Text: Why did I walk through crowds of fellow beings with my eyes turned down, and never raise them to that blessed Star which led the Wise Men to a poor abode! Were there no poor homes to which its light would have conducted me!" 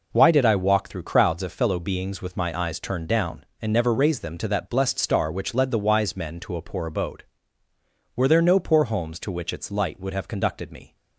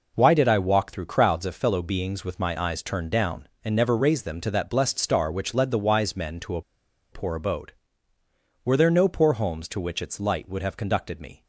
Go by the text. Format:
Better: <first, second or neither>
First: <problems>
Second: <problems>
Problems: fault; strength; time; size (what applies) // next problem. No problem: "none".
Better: first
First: none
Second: pauses between "a" and "poor"; noticeable; at 6.6 s; 0.51 s long